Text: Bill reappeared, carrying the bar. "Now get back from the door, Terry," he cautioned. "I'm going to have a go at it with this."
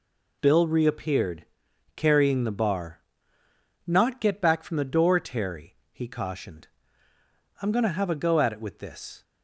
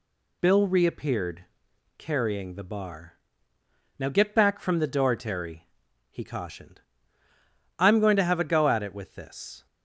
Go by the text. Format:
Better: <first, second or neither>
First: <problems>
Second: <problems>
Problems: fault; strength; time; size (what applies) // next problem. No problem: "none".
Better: second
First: says "Not" for "Now"; at 3.8 s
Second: none